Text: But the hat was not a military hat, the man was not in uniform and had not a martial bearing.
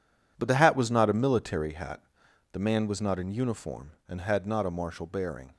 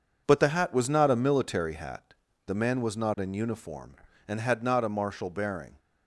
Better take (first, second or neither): second